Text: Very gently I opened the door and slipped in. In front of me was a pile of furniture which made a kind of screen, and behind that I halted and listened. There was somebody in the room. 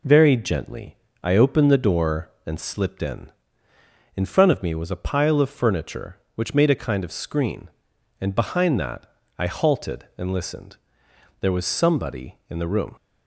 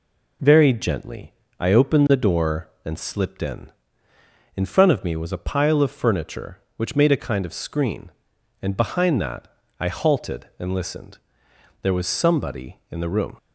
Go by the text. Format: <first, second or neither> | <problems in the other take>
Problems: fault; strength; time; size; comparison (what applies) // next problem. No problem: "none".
neither | pauses between "gently" and "I"; slight; the same in both // pauses between "that" and "I"; slight; the same in both